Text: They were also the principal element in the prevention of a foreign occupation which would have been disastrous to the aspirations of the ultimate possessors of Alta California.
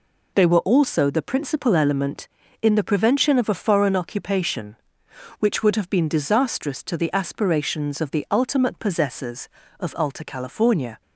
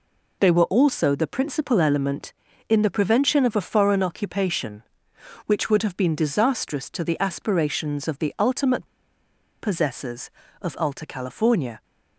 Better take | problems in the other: first | pauses between "ultimate" and "possessors"; noticeable; at 8.8 s; 0.74 s long

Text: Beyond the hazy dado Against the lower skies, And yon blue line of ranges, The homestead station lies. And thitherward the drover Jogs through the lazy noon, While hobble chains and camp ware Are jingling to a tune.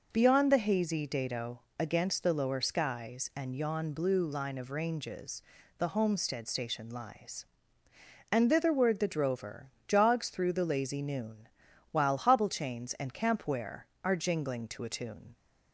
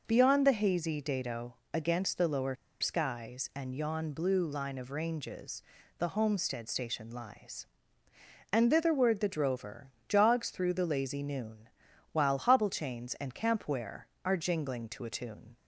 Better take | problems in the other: first | pauses between "dado" and "Against"; slight; at 1.5 s; 0.18 s long; slight in the first // pauses between "lower" and "skies"; slight; at 2.5 s; 0.25 s long // pauses between "drover" and "Jogs"; slight; at 9.8 s; 0.18 s long; slight in the first

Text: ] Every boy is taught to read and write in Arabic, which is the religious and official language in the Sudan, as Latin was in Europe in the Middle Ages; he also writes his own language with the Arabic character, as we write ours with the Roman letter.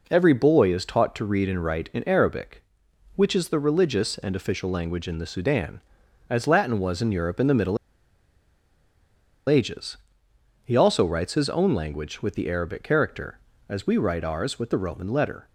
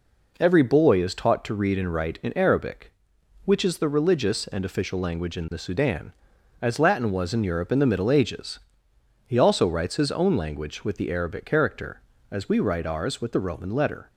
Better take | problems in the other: second | pauses between "Middle" and "Ages"; strong; at 7.7 s; 1.7 s long

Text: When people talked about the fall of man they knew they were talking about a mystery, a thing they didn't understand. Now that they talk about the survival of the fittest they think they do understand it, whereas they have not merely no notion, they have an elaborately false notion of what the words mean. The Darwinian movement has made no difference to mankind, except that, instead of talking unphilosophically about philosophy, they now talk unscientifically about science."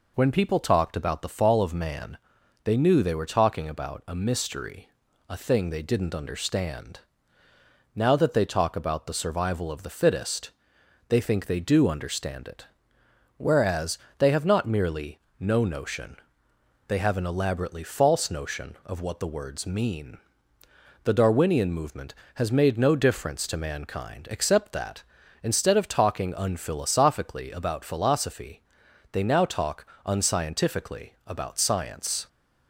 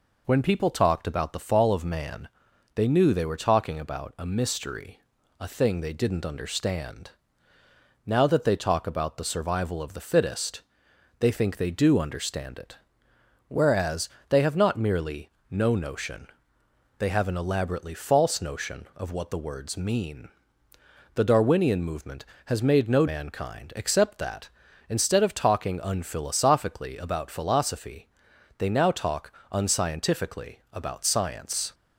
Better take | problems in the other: first | pauses between "man" and "they"; noticeable; at 2.2 s; 0.46 s long; noticeable in the first // pauses between "fittest" and "they"; noticeable; at 10.6 s; 0.58 s long; noticeable in the first // pauses between "whereas" and "they"; slight; at 14.0 s; 0.20 s long; slight in the first // pauses between "merely" and "no"; slight; at 15.2 s; 0.18 s long; slight in the first // skips "difference to"; at 23.0 s // pauses between "talk" and "unscientifically"; slight; at 29.3 s; 0.20 s long; slight in the first

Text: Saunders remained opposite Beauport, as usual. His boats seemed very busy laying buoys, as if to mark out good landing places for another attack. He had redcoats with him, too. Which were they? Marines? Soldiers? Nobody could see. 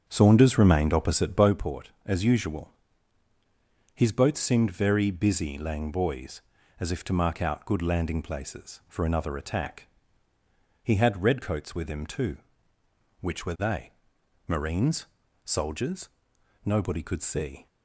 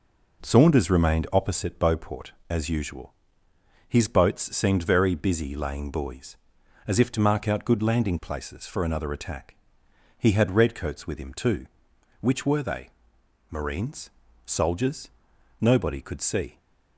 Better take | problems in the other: second | starts louder than the rest; strong; until 1.5 s; 7.5 dB

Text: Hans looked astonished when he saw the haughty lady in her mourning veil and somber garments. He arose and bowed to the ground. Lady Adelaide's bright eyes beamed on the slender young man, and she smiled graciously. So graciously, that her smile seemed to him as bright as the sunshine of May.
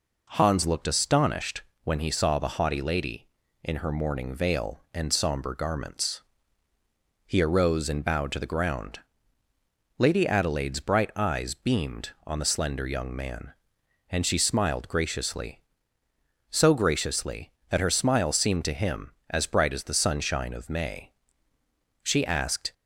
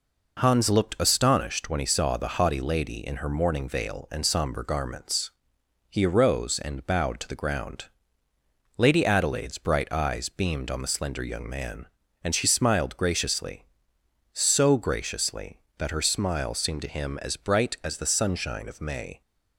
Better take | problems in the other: second | pauses between "astonished" and "when"; slight; at 1.6 s; 0.22 s long // goes on to say "She asked"; noticeable; from 22.0 s on; 0.70 s long

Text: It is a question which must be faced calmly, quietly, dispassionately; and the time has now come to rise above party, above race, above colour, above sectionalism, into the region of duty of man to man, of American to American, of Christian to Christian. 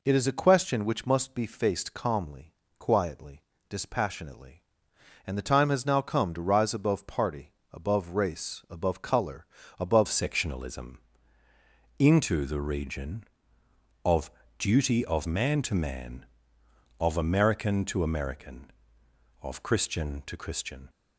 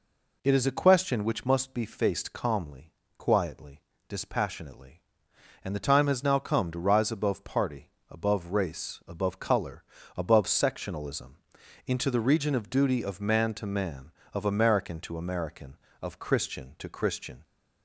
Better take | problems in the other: second | changes voice at "sectionalism"; from 10.0 s on; 10.8 s long // pauses between "of" and "duty"; slight; at 14.3 s; 0.26 s long

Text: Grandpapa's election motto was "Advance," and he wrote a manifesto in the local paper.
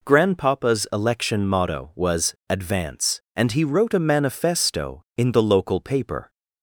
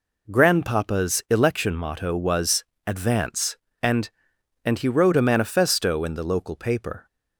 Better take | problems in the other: first | pauses between "was" and "Advance"; slight; at 2.6 s; 0.20 s long // says "and" twice; at 4.6 s

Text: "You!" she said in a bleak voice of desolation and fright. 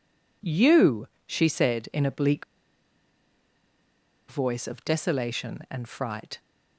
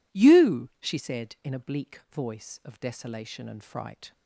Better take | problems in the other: second | pauses between "bleak" and "voice"; strong; at 2.4 s; 1.8 s long

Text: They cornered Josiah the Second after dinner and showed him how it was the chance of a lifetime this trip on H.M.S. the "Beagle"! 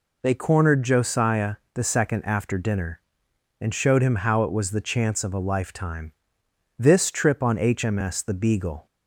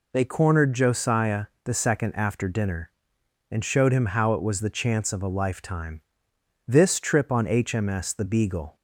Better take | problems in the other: neither | pauses between "Josiah" and "the"; slight; the same in both // pauses between "lifetime" and "this"; noticeable; the same in both

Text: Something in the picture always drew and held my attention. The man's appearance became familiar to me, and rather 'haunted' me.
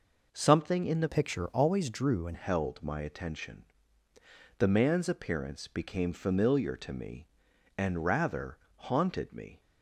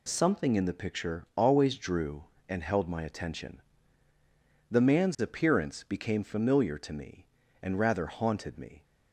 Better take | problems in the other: second | changes voice from "picture" to "and"; from 1.0 to 2.3 s; 1.3 s long // pauses between "rather" and "haunted"; slight; at 8.5 s; 0.20 s long

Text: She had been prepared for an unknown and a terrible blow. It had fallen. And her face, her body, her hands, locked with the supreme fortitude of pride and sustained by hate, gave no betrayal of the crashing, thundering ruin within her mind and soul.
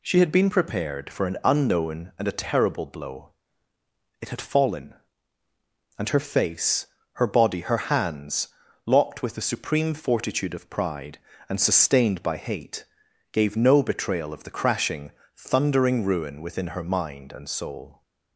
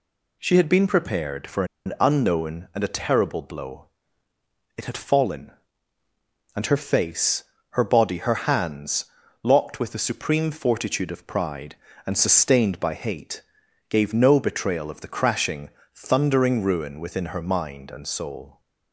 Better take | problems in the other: first | pauses between "for" and "an"; slight; at 1.6 s; 0.20 s long

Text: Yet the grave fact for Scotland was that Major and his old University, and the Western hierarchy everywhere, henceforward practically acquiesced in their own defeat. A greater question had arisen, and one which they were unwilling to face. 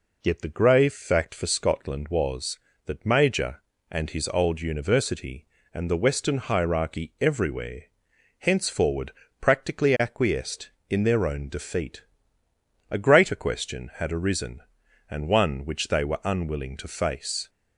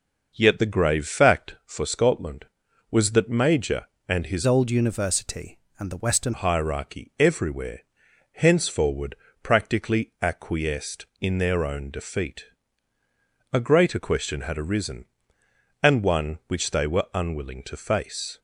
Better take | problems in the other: first | changes voice from "old" to "Western"; from 4.4 to 6.3 s; 1.9 s long // pauses between "henceforward" and "practically"; slight; at 9.1 s; 0.26 s long; slight in the first

